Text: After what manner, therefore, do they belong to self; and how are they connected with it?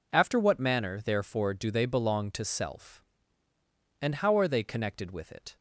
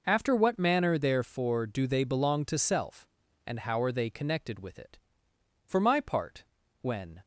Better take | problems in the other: first | goes on to say "For my part when"; from 5.6 s on; 1.5 s long

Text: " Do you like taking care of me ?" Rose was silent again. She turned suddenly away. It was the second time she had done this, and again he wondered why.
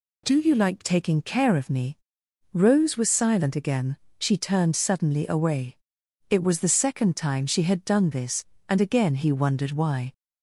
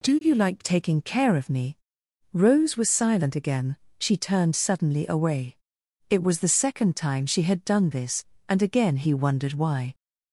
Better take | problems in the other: neither | none

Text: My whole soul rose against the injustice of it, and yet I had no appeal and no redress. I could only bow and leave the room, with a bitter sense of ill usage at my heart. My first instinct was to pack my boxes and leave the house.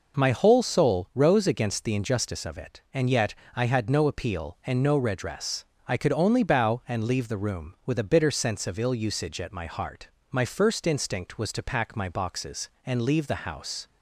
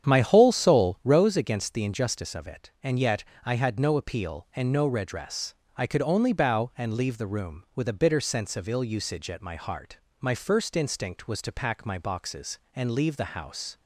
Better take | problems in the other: first | starts louder than the rest; strong; until 1.3 s; 9 dB // pauses between "yet" and "I"; slight; at 3.2 s; 0.20 s long; slight in the first

